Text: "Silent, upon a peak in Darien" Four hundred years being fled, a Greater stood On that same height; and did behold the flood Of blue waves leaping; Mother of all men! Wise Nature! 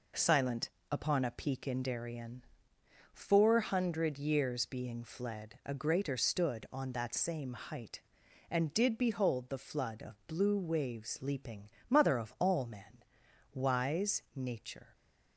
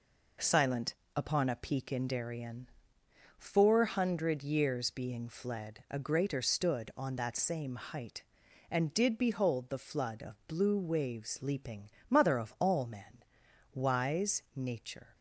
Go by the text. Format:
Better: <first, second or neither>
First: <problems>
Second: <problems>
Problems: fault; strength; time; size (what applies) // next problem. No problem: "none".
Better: neither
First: pauses between "Darien" and "Four"; noticeable; at 2.4 s; 0.68 s long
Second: pauses between "Darien" and "Four"; noticeable; at 2.6 s; 0.68 s long